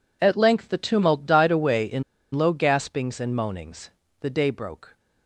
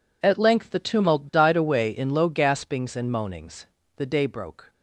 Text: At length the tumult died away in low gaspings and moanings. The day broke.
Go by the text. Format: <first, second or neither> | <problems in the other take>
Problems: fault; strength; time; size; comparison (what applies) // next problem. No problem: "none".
second | pauses between "in" and "low"; slight; at 2.0 s; 0.29 s long